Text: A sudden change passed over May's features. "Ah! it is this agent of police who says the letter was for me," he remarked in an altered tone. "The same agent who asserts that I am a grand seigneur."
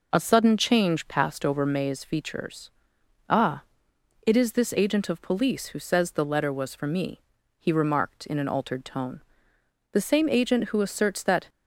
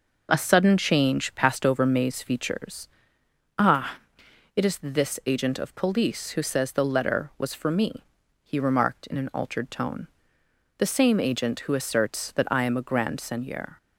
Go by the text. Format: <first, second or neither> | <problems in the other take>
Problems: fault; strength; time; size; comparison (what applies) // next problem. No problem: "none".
second | stops before "I am a grand seigneur"; at 11.4 s